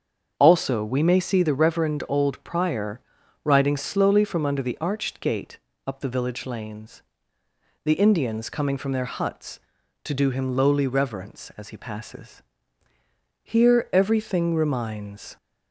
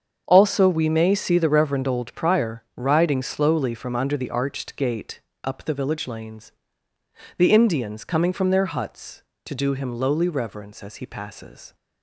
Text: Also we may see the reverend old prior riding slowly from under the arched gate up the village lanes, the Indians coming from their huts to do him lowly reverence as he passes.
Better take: second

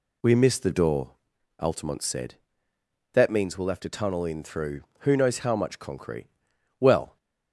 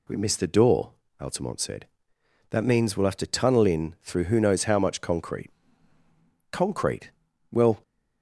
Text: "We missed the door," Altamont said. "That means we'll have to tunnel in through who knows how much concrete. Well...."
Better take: first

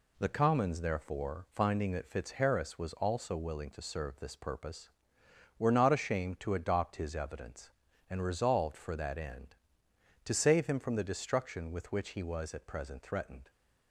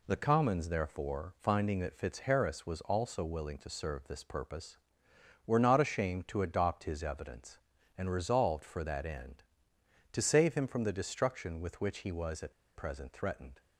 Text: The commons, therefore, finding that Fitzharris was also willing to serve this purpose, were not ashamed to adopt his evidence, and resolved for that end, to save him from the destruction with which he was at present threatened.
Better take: first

